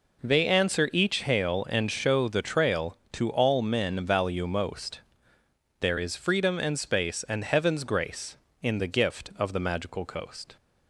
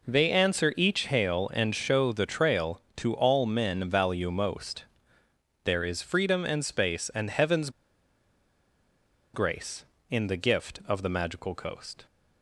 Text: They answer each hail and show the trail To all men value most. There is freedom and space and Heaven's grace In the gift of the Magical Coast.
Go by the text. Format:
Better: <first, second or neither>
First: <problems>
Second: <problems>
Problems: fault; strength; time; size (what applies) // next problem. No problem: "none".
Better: first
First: none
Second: pauses between "Heaven's" and "grace"; strong; at 7.6 s; 1.6 s long